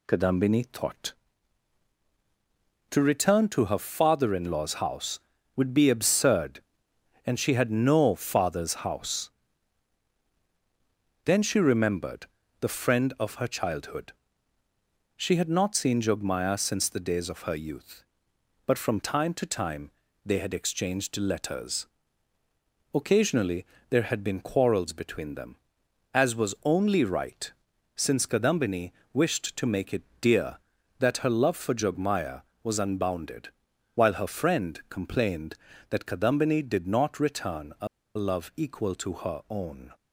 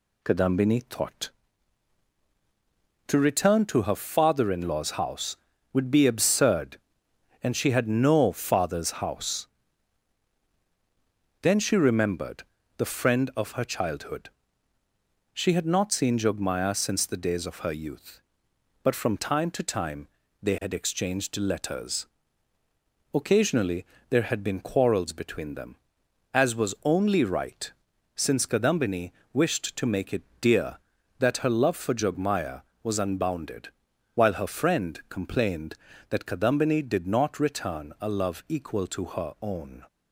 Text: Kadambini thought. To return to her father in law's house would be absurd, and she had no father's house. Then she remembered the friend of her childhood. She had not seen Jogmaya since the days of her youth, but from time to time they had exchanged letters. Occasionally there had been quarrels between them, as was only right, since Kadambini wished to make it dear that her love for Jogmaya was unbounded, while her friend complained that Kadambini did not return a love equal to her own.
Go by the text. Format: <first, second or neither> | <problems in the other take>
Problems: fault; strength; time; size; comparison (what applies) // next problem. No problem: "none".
second | pauses between "remembered" and "the"; slight; at 12.2 s; 0.34 s long; slight in the second // pauses between "time" and "they"; slight; at 19.9 s; 0.34 s long; slight in the second // pauses between "Occasionally" and "there"; slight; at 23.6 s; 0.24 s long; slight in the second // pauses between "Kadambini" and "wished"; slight; at 28.9 s; 0.22 s long; slight in the second // pauses between "it" and "dear"; slight; at 30.0 s; 0.16 s long; slight in the second // pauses between "a" and "love"; slight; at 37.8 s; 0.29 s long